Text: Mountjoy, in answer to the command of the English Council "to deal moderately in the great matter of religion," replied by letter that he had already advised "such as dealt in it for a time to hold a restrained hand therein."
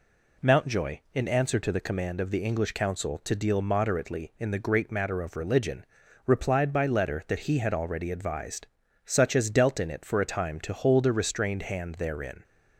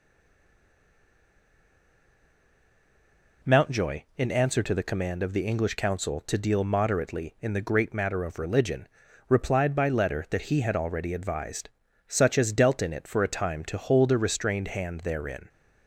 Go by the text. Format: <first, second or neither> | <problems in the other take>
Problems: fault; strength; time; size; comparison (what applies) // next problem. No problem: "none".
first | stays silent before the first word; strong; until 3.4 s; 3.4 s long // pauses between "advised" and "such"; slight; at 11.7 s; 0.36 s long; slight in the first